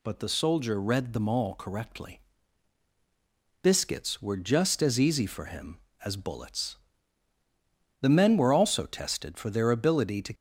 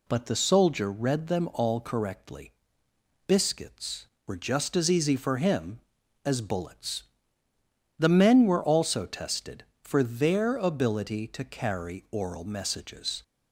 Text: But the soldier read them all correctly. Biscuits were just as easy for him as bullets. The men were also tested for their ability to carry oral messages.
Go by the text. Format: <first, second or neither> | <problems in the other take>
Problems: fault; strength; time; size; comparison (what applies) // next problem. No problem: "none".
second | stops before "carry oral messages"; at 10.3 s